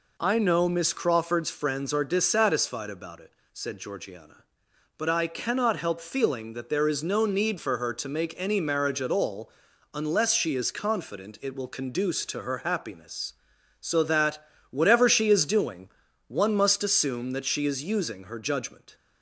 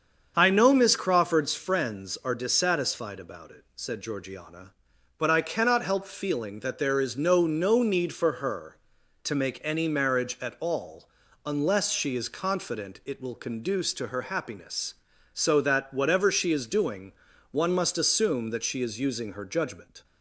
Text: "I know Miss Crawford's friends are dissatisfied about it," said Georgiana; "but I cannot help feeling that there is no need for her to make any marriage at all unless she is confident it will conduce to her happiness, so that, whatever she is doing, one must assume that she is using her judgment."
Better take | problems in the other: first | starts louder than the rest; until 1.3 s; 7 dB // says "no" twice; at 7.4 s // pauses between "all" and "unless"; at 11.0 s; 0.38 s long; also in the first

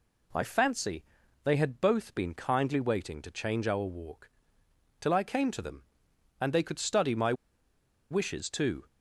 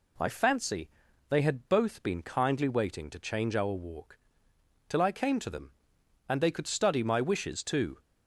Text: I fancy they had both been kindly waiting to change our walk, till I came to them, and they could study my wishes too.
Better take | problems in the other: second | pauses between "fancy" and "they"; at 1.0 s; 0.40 s long; also in the second // pauses between "my" and "wishes"; noticeable; at 7.3 s; 0.77 s long

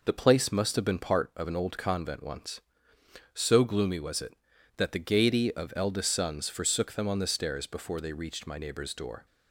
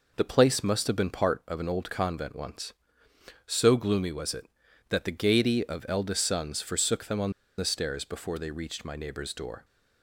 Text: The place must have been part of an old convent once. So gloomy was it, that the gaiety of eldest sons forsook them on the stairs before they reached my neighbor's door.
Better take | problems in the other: first | pauses between "on" and "the"; slight; at 7.3 s; 0.26 s long

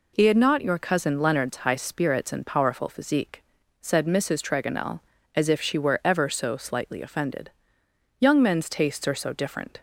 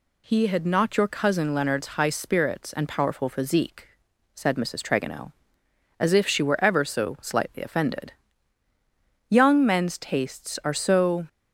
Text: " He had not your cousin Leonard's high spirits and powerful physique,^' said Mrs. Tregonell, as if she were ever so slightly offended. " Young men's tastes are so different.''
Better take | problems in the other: first | stops before "different"; at 11.2 s

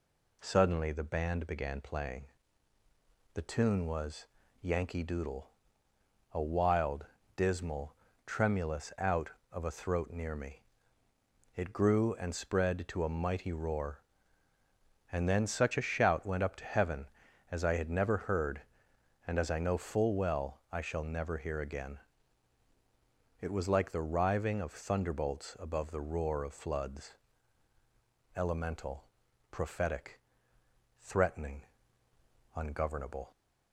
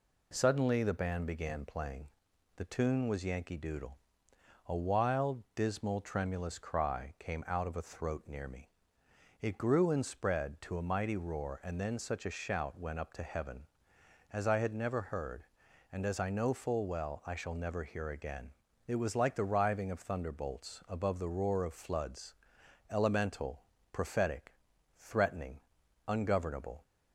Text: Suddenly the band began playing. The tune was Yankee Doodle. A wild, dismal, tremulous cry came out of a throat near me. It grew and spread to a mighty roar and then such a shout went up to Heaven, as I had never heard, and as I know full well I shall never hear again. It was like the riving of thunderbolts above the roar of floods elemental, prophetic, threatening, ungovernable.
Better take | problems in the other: second | pauses between "was" and "Yankee"; slight; at 4.2 s; 0.34 s long // skips "cry came"; at 8.9 s // pauses between "floods" and "elemental"; at 27.1 s; 1.2 s long; noticeable in the second

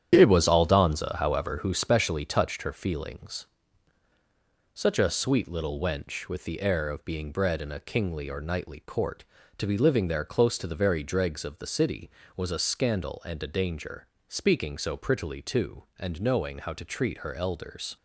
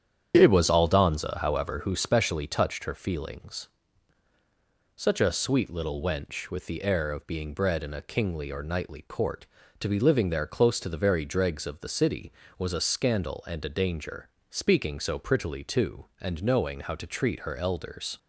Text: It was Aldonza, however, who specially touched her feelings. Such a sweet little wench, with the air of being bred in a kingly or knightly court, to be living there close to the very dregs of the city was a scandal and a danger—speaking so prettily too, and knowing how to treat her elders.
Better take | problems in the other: second | gets quieter; strong; throughout; 7 dB // starts louder than the rest; strong; until 1.1 s; 9.5 dB; strong in the second

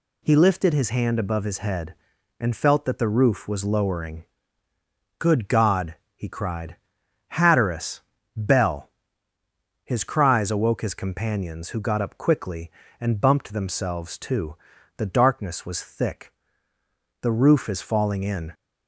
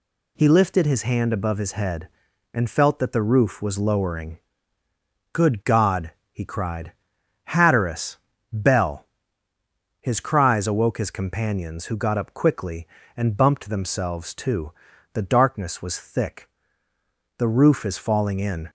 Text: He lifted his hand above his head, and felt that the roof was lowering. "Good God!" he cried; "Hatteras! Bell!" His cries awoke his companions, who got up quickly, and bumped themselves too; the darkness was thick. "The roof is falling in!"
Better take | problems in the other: neither | none

